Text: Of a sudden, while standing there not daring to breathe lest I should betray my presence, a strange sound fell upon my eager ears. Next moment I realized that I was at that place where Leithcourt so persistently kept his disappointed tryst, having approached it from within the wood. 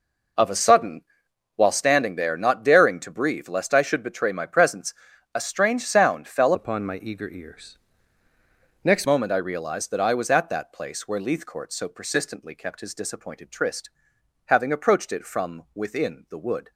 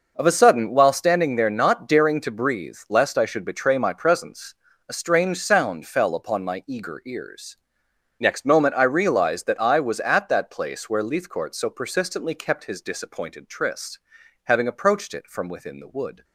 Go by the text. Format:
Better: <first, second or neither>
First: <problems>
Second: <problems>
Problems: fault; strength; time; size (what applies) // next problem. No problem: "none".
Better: second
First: changes voice from "upon" to "Next"; from 6.5 to 9.0 s; 2.5 s long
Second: none